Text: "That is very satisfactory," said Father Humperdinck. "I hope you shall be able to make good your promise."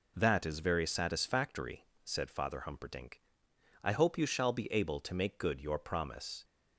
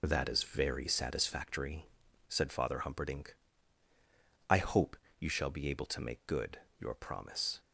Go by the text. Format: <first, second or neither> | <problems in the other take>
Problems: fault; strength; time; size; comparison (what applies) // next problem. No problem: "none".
first | loses the start of "That"; at 0.0 s; 25 ms // pauses between "hope" and "you"; slight; at 4.9 s; 0.24 s long // pauses between "good" and "your"; slight; at 6.5 s; 0.22 s long